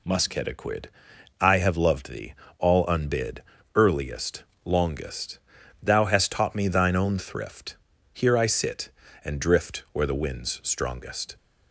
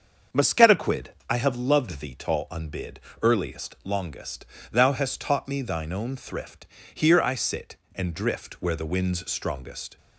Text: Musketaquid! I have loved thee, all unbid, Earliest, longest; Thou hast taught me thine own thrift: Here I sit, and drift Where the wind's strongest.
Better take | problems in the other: first | starts louder than the rest; until 1.5 s; 7 dB // says "tall" for "all"; at 2.1 s

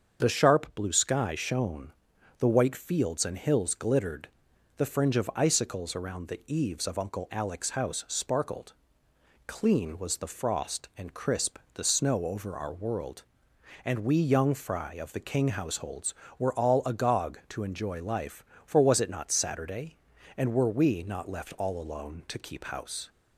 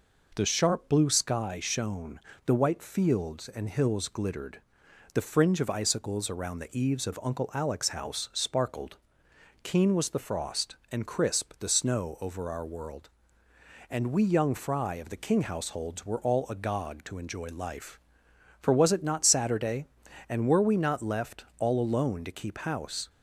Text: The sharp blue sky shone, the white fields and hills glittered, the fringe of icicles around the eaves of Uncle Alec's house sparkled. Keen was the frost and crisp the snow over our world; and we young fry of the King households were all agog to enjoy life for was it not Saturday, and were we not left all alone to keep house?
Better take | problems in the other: second | starts louder than the rest; until 1.2 s; 7 dB // says "Clean" for "Keen"; at 9.4 s // pauses between "crisp" and "the"; slight; at 11.5 s; 0.16 s long

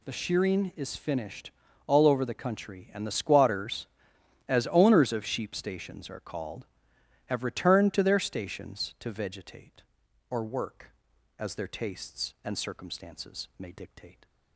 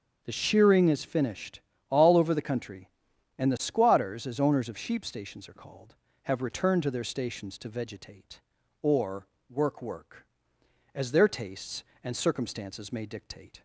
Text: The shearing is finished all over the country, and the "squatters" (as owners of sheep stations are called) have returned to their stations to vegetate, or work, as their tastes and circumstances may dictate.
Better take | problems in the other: first | starts louder than the rest; until 1.2 s; 7 dB // pauses between "finished" and "all"; slight; at 1.6 s; 0.28 s long; slight in the first // pauses between "or" and "work"; slight; at 9.2 s; 0.24 s long // says "work" twice; at 9.8 s

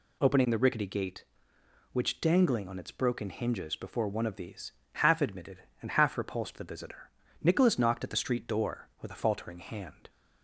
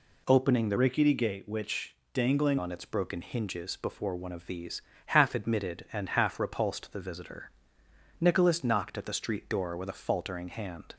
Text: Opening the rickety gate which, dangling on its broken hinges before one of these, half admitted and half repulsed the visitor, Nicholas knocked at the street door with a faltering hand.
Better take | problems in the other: first | changes voice from "rickety" to "dangling"; from 0.7 to 2.5 s; 1.8 s long

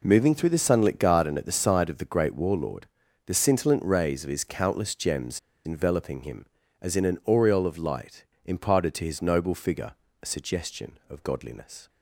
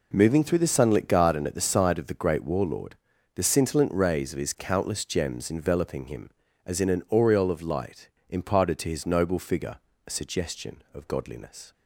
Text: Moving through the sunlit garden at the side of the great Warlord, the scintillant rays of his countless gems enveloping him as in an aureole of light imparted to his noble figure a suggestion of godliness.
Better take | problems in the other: second | pauses between "gems" and "enveloping"; slight; at 5.3 s; 0.26 s long // pauses between "light" and "imparted"; slight; at 8.2 s; 0.20 s long; slight in the second // pauses between "figure" and "a"; slight; at 9.9 s; 0.30 s long; slight in the second

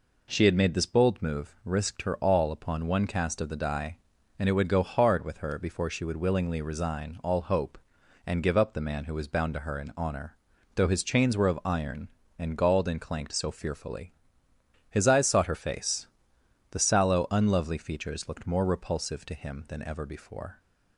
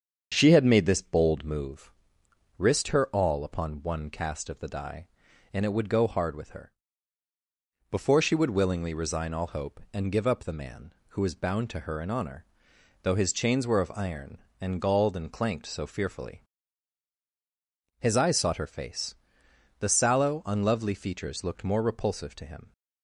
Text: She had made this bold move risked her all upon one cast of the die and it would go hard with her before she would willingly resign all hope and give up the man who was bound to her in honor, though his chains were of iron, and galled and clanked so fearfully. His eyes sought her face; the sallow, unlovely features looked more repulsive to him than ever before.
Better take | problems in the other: first | starts louder than the rest; strong; until 1.3 s; 7.5 dB // pauses between "move" and "risked"; noticeable; at 1.9 s; 0.64 s long // pauses between "her" and "before"; at 6.7 s; 1.1 s long // stops before "than ever before"; at 22.7 s

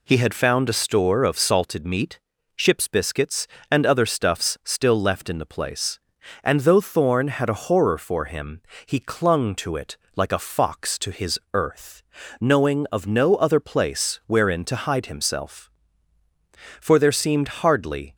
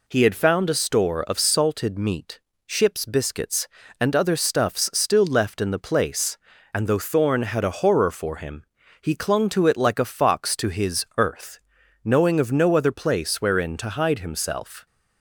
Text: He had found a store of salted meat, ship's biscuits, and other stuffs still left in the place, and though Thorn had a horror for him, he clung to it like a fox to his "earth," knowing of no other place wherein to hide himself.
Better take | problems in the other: second | pauses between "it" and "like"; slight; at 9.9 s; 0.18 s long // pauses between "his" and "earth"; slight; at 11.3 s; 0.16 s long // goes on to say "For there seemed hardly"; from 16.8 s on; 1.3 s long

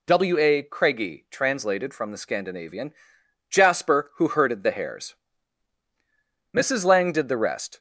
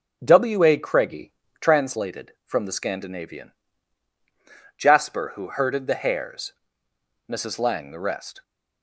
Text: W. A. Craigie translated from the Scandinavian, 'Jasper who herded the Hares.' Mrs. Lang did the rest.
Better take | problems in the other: first | pauses between "Craigie" and "translated"; slight; at 1.3 s; 0.28 s long // skips "did"; at 7.9 s

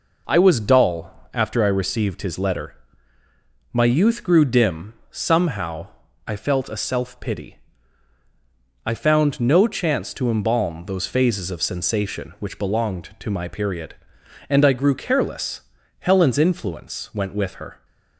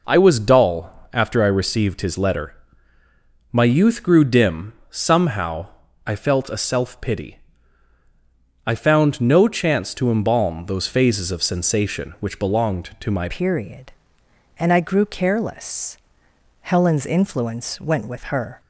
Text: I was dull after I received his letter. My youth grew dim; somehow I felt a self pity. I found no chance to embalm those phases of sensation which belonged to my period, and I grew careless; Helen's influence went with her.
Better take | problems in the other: first | pauses between "somehow" and "I"; at 5.6 s; 0.40 s long; also in the first // changes voice at "period"; from 13.3 s on; 5.2 s long

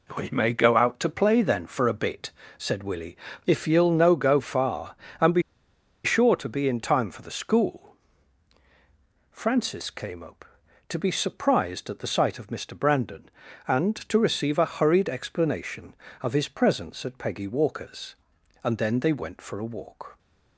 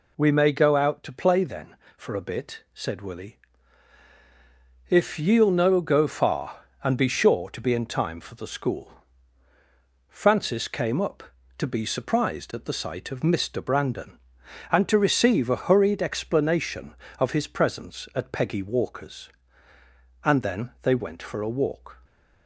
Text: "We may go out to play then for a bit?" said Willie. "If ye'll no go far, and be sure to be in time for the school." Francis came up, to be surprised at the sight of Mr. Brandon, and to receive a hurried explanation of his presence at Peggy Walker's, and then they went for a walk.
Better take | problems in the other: second | pauses between "be" and "sure"; noticeable; at 5.4 s; 0.62 s long

